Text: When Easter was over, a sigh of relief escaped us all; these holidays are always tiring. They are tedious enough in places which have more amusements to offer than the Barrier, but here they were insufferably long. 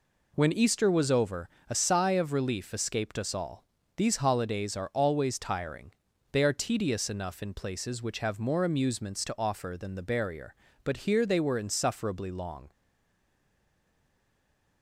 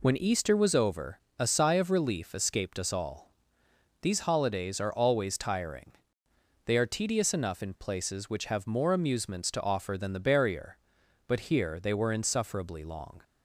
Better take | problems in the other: second | stays silent after the last word; from 12.7 s on; 2.1 s long

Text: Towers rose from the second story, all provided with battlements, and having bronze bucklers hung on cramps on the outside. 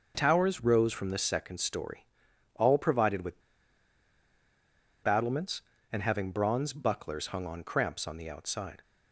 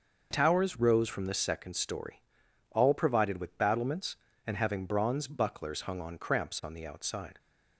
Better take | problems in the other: second | starts louder than the rest; noticeable; until 1.1 s; 6 dB; noticeable in the second // pauses between "with" and "battlements"; strong; at 3.3 s; 1.6 s long

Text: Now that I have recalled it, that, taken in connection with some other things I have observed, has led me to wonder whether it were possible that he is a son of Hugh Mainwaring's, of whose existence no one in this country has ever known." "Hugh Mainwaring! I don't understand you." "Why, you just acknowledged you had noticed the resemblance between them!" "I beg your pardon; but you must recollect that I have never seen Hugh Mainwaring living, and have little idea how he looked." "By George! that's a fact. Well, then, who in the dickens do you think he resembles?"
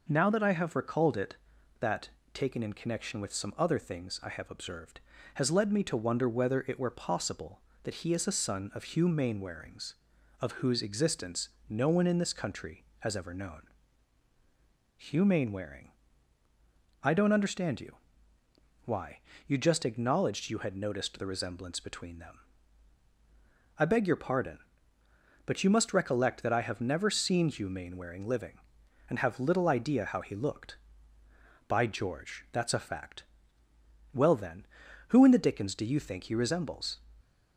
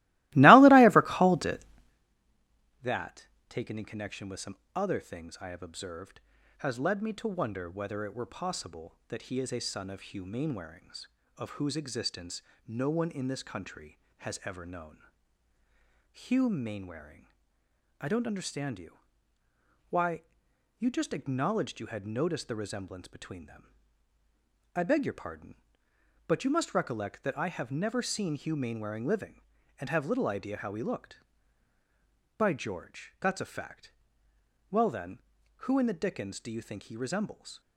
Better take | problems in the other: first | starts louder than the rest; strong; until 2.1 s; 20 dB // pauses between "some" and "other"; slight; at 4.5 s; 0.20 s long // pauses between "existence" and "no"; slight; at 12.4 s; 0.26 s long; slight in the first

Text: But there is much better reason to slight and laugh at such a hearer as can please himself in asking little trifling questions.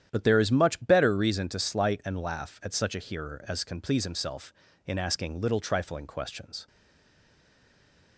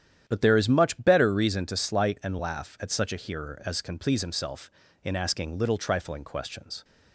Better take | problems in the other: second | starts louder than the rest; strong; until 1.1 s; 10 dB; strong in the second // stays silent after the last word; noticeable; from 6.6 s on; 1.5 s long

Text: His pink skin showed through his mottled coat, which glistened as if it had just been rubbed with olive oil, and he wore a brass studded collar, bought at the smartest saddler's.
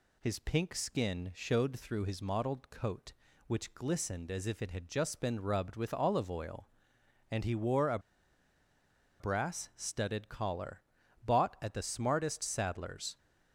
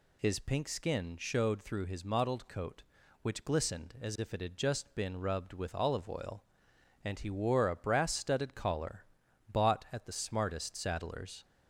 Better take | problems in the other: second | pauses between "a" and "brass"; at 7.9 s; 1.2 s long

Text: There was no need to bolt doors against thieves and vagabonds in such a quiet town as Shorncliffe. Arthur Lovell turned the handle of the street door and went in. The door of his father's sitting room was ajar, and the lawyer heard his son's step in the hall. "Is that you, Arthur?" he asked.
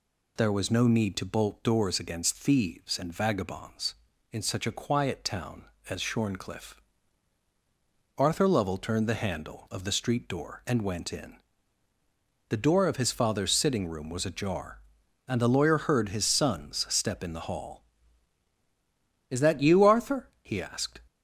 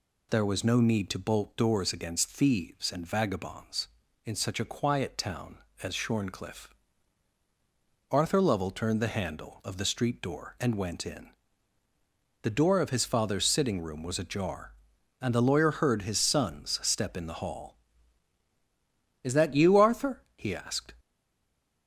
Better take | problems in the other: first | stays silent after the last word; slight; from 20.9 s on; 0.9 s long

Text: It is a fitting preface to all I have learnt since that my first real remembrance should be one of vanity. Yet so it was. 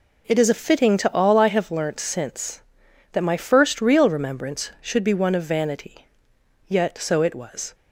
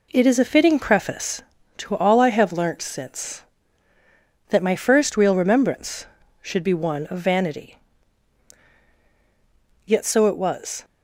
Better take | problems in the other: second | skips "preface"; at 0.9 s

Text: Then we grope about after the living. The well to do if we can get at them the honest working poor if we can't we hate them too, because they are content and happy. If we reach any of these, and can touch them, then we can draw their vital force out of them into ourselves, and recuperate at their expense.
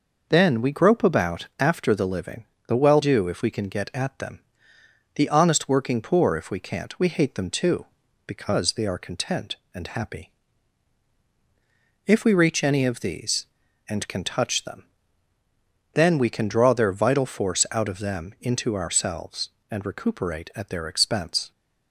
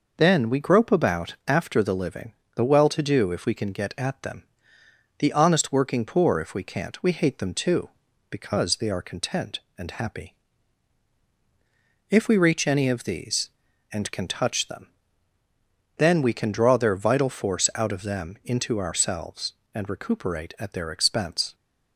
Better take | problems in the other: second | skips "to"; at 3.0 s // pauses between "them" and "the"; noticeable; at 4.4 s; 0.74 s long; noticeable in the second

